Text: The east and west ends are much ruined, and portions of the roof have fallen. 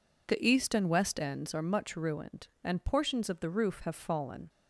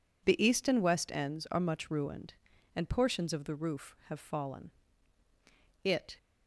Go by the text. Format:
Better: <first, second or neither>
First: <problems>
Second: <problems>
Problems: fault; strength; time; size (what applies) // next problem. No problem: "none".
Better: first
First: none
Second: goes on to say "It"; slight; from 5.8 s on; 0.34 s long